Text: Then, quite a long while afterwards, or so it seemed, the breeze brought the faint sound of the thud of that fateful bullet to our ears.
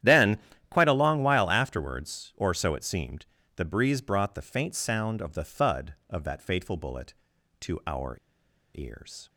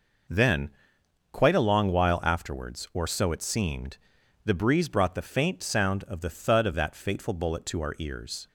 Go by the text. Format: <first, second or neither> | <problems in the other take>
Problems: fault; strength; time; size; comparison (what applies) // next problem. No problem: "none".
second | starts louder than the rest; strong; until 1.3 s; 11 dB // pauses between "our" and "ears"; noticeable; at 8.1 s; 0.57 s long